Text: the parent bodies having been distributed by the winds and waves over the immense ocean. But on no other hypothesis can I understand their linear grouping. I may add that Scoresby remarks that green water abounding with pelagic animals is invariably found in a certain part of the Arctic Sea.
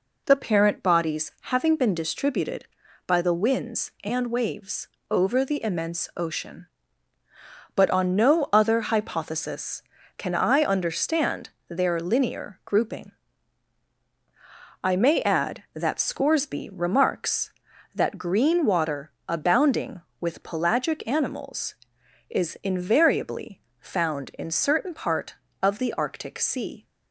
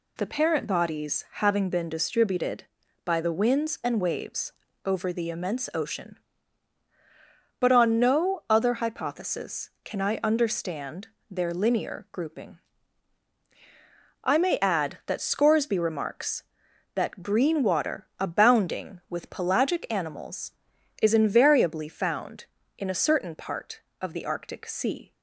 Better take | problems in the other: second | pauses between "waves" and "over"; slight; at 4.8 s; 0.24 s long; slight in the second // pauses between "understand" and "their"; slight; at 11.4 s; 0.20 s long; slight in the second // pauses between "water" and "abounding"; slight; at 19.1 s; 0.16 s long // pauses between "invariably" and "found"; slight; at 23.6 s; 0.20 s long // skips "a"; at 24.5 s

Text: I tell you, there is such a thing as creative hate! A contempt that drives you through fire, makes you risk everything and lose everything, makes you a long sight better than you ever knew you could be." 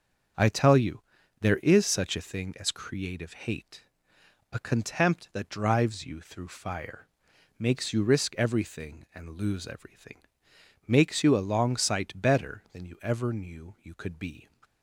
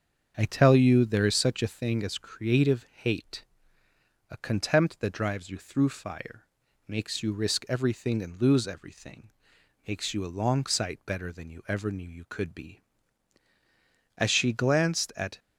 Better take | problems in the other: first | starts louder than the rest; strong; until 1.3 s; 7 dB; strong in the first // goes on to say "As she glanced at"; noticeable; from 14.1 s on; 1.2 s long

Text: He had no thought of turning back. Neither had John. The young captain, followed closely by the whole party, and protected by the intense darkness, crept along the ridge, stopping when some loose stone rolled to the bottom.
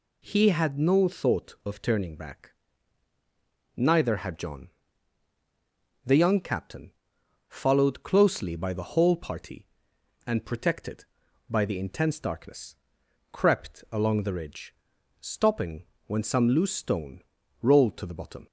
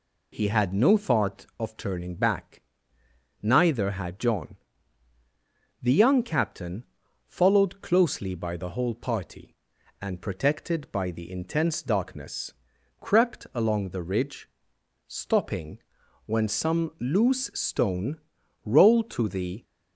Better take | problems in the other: first | pauses between "stopping" and "when"; noticeable; at 15.7 s; 0.48 s long; slight in the first // pauses between "stone" and "rolled"; noticeable; at 18.1 s; 0.48 s long; also in the first // stops before "bottom"; at 19.6 s

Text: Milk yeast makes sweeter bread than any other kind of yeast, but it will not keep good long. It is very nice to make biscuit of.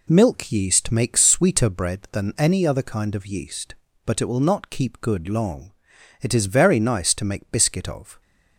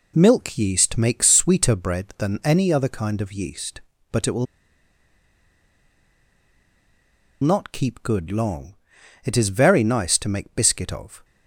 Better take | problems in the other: first | pauses between "will" and "not"; strong; at 4.4 s; 2.9 s long

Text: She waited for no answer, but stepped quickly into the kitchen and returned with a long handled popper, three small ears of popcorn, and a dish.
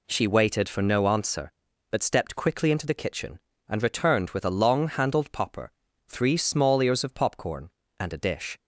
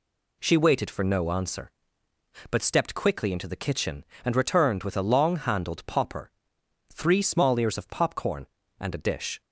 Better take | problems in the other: neither | none

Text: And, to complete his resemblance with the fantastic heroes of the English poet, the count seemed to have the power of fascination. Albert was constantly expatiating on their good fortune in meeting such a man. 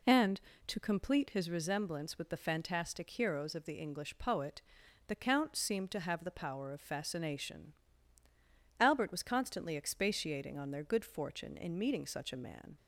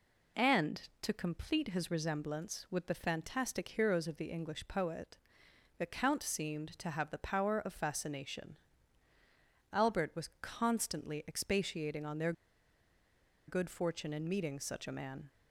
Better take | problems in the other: first | pauses between "their" and "good"; at 12.3 s; 1.1 s long

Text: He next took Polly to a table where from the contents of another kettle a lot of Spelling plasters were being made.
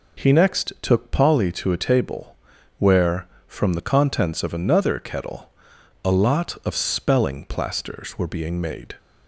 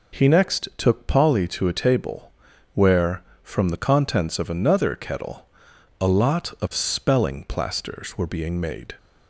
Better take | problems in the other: neither | pauses between "table" and "where"; noticeable; the same in both // pauses between "kettle" and "a"; noticeable; the same in both

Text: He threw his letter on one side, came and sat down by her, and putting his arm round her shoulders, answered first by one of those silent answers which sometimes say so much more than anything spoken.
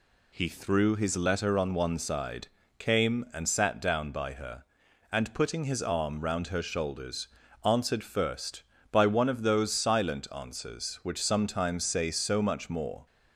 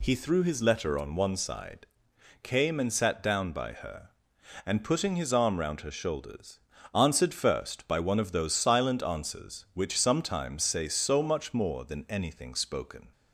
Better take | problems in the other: second | stops before "than anything spoken"; at 13.0 s

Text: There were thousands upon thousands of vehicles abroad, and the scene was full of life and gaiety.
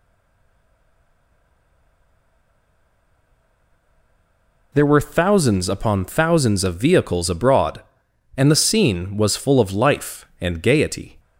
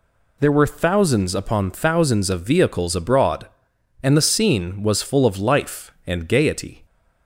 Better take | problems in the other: second | stays silent before the first word; strong; until 4.7 s; 4.7 s long

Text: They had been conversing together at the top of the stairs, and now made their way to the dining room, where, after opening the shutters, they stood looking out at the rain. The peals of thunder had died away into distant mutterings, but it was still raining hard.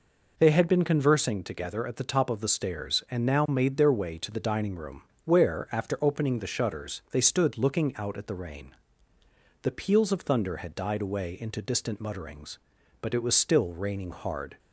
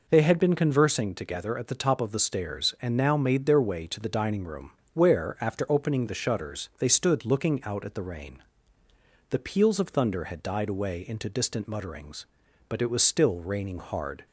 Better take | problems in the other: neither | none

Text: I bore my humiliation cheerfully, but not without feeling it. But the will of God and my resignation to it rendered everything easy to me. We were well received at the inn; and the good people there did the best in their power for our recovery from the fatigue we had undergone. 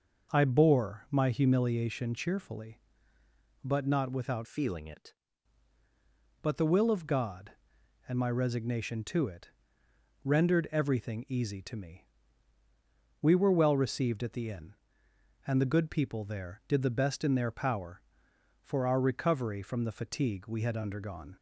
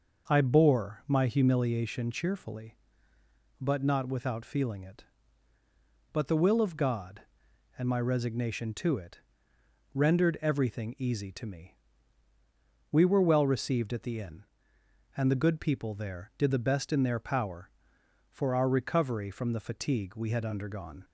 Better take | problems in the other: second | changes voice from "feeling" to "it"; from 4.4 to 5.1 s; 0.7 s long // pauses between "it" and "rendered"; noticeable; at 9.4 s; 0.74 s long; noticeable in the second

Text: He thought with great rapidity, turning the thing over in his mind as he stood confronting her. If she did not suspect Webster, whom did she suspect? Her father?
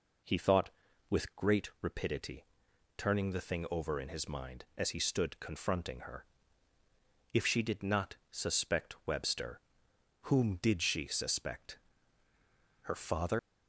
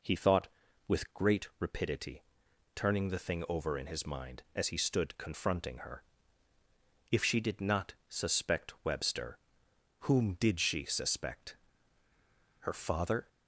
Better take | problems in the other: second | leaves "father" unfinished; at 13.3 s; 110 ms

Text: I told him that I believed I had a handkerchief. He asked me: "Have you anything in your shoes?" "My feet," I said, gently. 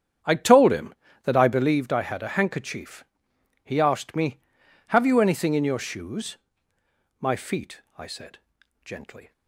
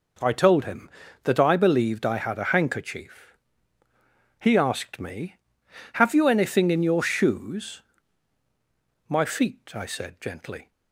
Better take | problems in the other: second | starts louder than the rest; strong; until 1.8 s; 8.5 dB

